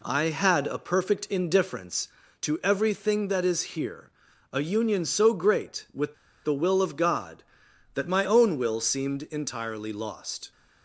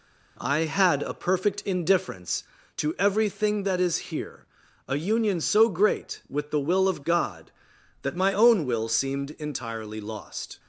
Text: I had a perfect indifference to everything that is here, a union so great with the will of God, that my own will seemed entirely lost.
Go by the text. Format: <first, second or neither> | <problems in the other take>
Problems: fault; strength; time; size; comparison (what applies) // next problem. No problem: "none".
second | pauses between "is" and "here"; slight; at 3.6 s; 0.16 s long; slight in the second // pauses between "with" and "the"; slight; at 6.1 s; 0.29 s long